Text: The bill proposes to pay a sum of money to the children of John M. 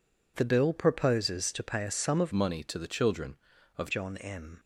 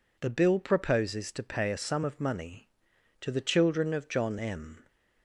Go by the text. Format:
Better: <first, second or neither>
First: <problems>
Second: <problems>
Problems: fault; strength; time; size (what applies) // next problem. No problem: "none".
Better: second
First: changes voice from "money" to "of"; from 2.3 to 3.9 s; 1.6 s long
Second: none